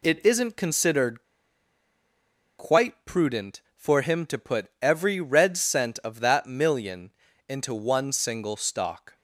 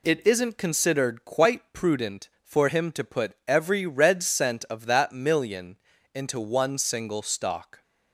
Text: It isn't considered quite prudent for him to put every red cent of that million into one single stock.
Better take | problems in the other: second | pauses between "considered" and "quite"; strong; at 1.2 s; 1.3 s long // pauses between "million" and "into"; at 7.1 s; 0.38 s long; also in the second

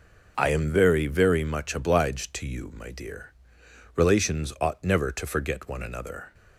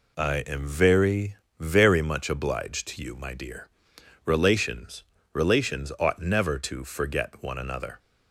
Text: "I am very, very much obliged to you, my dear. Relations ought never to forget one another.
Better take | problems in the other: first | says "Relations" twice; at 5.3 s

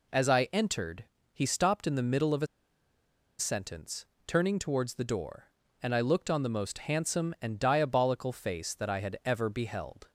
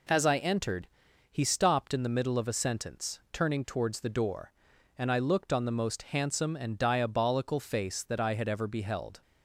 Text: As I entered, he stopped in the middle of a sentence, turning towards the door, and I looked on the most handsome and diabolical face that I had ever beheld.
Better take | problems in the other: second | pauses between "a" and "sentence"; noticeable; at 2.4 s; 0.92 s long

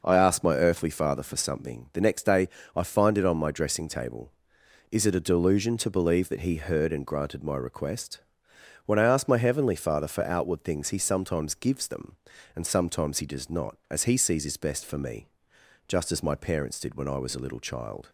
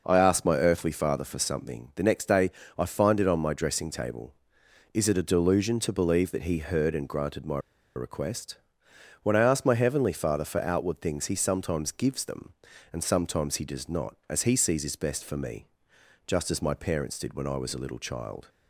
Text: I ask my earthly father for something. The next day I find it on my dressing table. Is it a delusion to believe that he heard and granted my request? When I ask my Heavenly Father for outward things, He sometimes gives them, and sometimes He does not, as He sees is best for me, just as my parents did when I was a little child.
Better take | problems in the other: first | pauses between "day" and "I"; slight; at 2.4 s; 0.28 s long; slight in the first // pauses between "my" and "request"; at 7.5 s; 0.38 s long

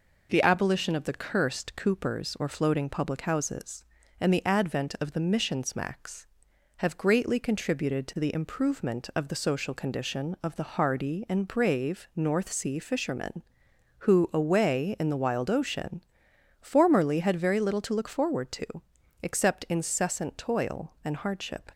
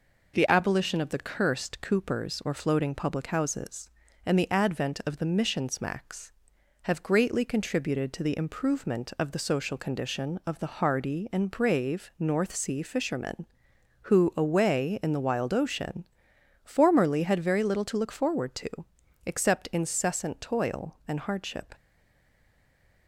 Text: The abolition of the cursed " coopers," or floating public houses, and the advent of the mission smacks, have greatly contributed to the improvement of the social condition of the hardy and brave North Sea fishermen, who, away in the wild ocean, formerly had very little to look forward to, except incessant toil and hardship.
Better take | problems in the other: first | stays silent after the last word; noticeable; from 21.7 s on; 1.3 s long

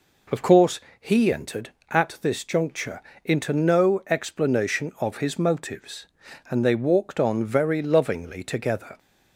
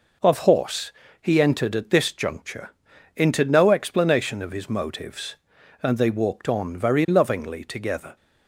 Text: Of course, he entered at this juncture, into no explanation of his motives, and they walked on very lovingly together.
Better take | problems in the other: first | says "horse" for "course"; at 0.3 s

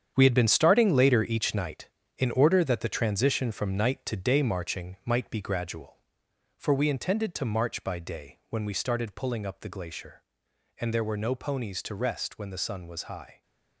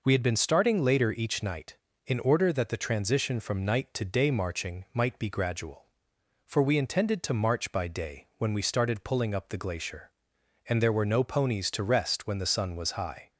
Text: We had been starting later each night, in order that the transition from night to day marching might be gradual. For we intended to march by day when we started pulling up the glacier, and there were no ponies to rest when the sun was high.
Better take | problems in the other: second | gets quieter; strong; throughout; 10.5 dB

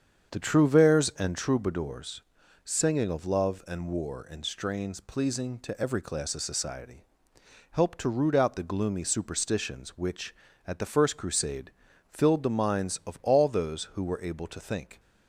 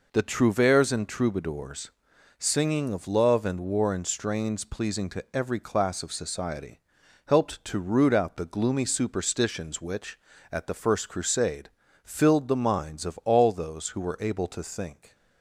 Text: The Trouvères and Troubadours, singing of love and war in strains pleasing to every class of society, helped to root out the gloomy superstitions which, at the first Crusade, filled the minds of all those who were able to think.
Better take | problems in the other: second | starts louder than the rest; strong; until 1.4 s; 7.5 dB

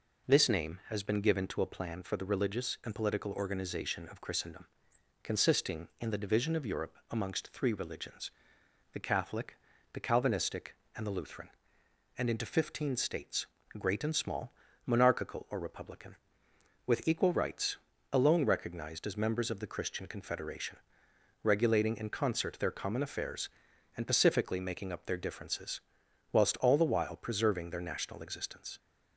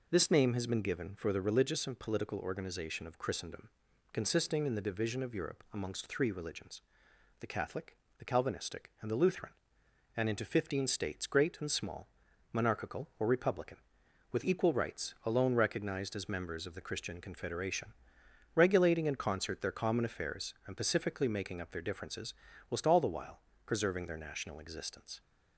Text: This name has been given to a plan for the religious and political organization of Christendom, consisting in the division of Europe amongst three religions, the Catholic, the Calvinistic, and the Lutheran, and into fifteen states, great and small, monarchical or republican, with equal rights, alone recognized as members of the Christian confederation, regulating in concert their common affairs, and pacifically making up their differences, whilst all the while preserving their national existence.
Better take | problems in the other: first | skips "to a plan"; at 1.1 s // pauses between "while" and "preserving"; slight; at 23.4 s; 0.26 s long

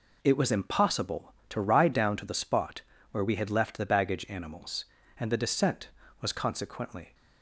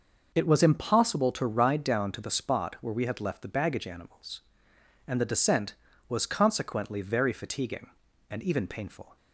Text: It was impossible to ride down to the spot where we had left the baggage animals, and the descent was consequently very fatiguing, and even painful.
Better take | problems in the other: second | pauses between "spot" and "where"; slight; at 2.8 s; 0.30 s long // stops before "very fatiguing and even painful"; at 7.1 s

